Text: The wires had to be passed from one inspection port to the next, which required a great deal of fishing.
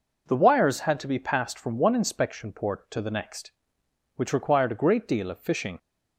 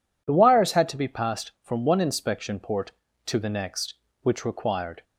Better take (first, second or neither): first